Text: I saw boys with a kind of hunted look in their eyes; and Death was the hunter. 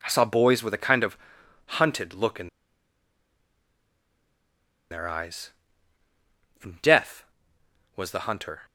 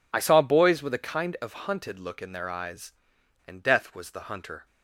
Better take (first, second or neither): second